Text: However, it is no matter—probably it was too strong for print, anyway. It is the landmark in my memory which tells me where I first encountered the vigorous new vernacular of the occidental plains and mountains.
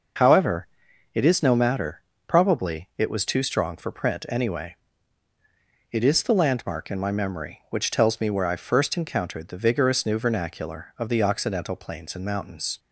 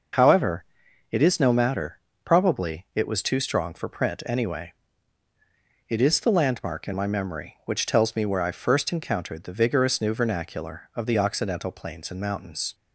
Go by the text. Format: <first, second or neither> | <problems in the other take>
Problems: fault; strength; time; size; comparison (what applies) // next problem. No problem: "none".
neither | none